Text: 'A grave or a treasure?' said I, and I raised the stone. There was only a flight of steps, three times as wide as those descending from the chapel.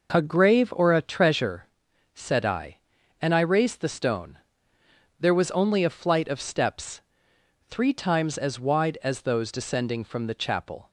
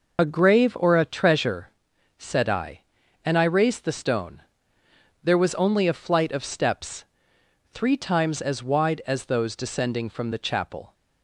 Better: first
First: none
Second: loses the start of "A"; at 0.1 s; 55 ms

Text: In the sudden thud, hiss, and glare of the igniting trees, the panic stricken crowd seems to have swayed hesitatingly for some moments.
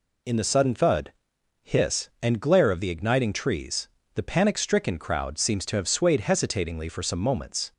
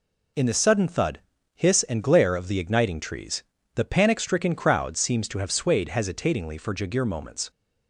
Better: first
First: none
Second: says "jagir" for "some"; at 6.7 s

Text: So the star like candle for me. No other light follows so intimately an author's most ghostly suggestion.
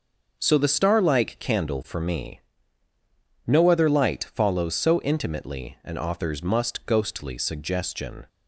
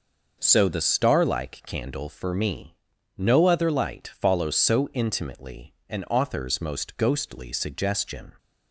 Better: second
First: starts louder than the rest; until 1.4 s; 6.5 dB // says "must" for "most"; at 6.4 s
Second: none

